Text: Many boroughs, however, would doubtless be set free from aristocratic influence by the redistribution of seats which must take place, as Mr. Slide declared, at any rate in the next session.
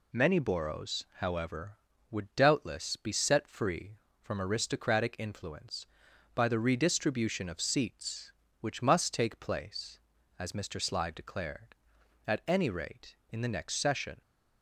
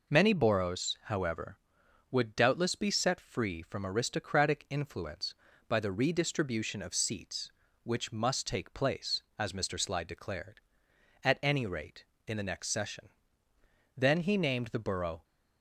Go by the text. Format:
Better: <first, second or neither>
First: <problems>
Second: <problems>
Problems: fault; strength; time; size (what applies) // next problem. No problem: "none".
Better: first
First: none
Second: goes on to say "Then he named the borough"; noticeable; from 13.9 s on; 1.2 s long